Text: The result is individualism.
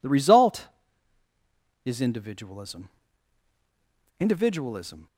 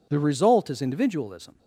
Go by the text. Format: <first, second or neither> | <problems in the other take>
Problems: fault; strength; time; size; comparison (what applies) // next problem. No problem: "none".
second | says "individualism" twice; at 4.1 s